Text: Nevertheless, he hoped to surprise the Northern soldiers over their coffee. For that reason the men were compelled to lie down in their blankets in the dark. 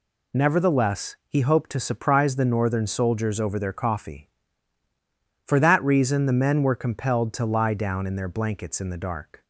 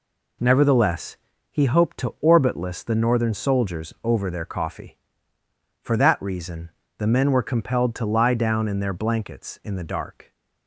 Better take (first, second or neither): first